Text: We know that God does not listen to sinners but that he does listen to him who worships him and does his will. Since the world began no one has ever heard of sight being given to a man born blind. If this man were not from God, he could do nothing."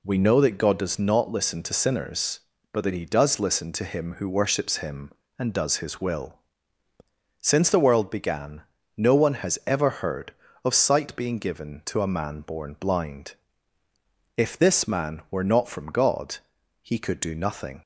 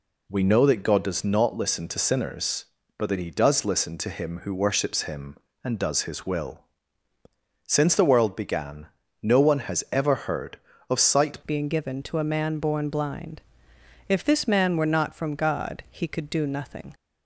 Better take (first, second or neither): first